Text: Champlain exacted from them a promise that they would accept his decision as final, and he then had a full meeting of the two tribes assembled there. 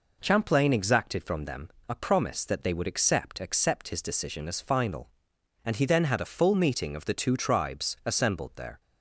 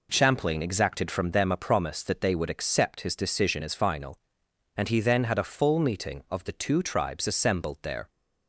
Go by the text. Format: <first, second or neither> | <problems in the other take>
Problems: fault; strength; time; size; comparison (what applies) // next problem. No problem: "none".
second | pauses between "them" and "a"; slight; at 1.6 s; 0.18 s long // says "accept" twice; at 3.3 s